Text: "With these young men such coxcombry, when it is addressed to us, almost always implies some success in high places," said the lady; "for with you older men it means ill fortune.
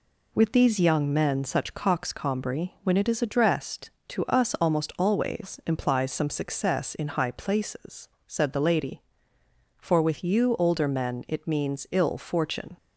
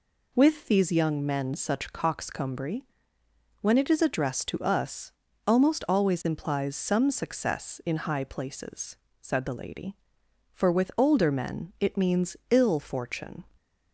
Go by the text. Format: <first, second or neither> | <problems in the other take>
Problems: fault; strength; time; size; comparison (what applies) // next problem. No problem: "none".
first | skips "you"; at 10.9 s